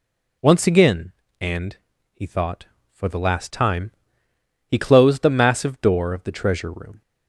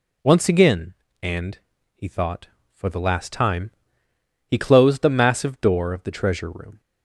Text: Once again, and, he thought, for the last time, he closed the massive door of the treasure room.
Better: neither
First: none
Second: none

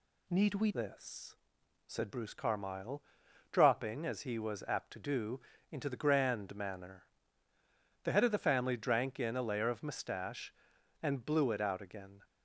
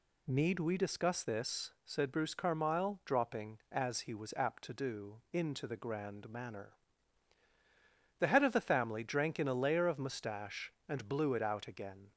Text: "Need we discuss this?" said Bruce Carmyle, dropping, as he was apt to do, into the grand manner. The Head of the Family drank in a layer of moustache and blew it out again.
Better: second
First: skips "discuss"; at 0.7 s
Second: none

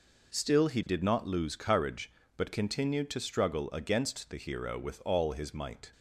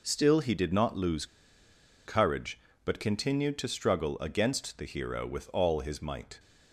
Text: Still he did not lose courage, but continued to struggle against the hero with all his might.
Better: first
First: none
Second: pauses between "lose" and "courage"; noticeable; at 1.2 s; 0.80 s long

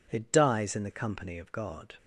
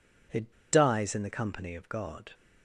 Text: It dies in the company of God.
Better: first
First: none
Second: pauses between "It" and "dies"; slight; at 0.5 s; 0.18 s long

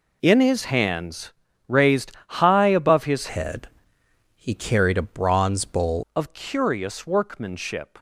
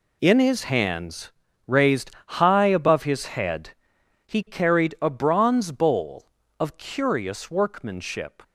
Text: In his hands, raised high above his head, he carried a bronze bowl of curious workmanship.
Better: second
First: pauses between "raised" and "high"; slight; at 2.1 s; 0.16 s long // changes voice from "head" to "bowl"; from 3.2 to 6.0 s; 2.8 s long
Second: pauses between "raised" and "high"; slight; at 2.1 s; 0.16 s long

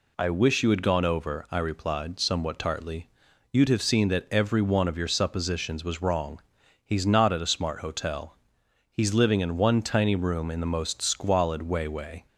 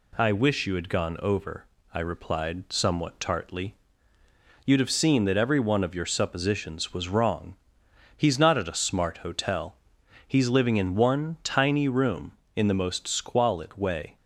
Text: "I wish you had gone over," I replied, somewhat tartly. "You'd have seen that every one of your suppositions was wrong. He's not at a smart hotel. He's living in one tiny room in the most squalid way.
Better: second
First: says "way" twice; at 11.8 s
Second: none

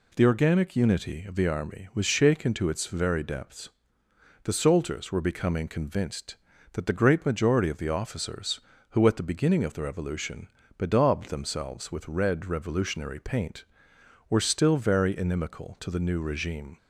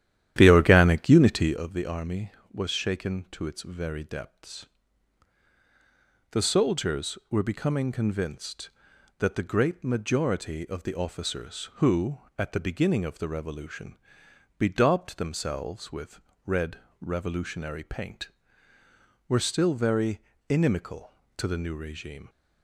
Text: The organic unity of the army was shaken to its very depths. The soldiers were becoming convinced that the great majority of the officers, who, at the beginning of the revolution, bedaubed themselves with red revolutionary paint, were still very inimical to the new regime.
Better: first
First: none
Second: starts louder than the rest; strong; until 1.6 s; 11.5 dB // pauses between "with" and "red"; slight; at 16.1 s; 0.26 s long // pauses between "red" and "revolutionary"; slight; at 16.7 s; 0.24 s long // pauses between "very" and "inimical"; slight; at 20.1 s; 0.30 s long

